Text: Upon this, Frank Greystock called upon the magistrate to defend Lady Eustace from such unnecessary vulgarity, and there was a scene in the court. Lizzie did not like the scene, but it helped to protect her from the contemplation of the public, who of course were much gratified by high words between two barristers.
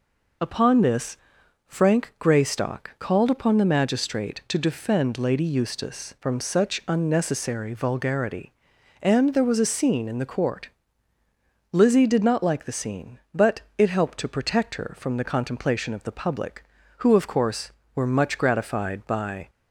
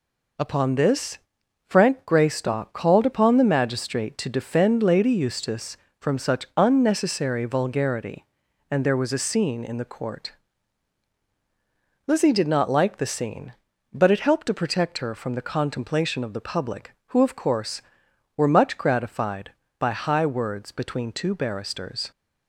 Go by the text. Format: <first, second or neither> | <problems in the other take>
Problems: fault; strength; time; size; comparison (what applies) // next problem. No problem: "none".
second | pauses between "but" and "it"; slight; at 13.6 s; 0.16 s long // stops before "high words between two barristers"; at 19.4 s